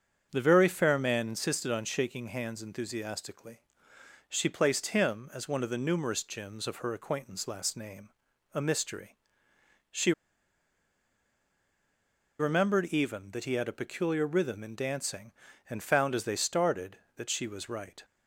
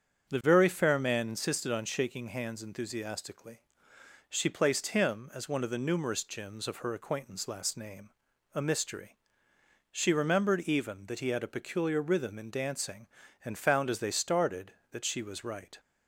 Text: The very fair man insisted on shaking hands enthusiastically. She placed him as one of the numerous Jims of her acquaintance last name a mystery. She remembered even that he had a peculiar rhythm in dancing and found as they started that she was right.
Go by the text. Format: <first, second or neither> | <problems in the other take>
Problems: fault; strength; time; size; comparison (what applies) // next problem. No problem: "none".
second | starts louder than the rest; strong; until 1.3 s; 7 dB; strong in the second // pauses between "name" and "a"; at 8.0 s; 0.44 s long; also in the second // pauses between "She" and "remembered"; strong; at 10.1 s; 2.2 s long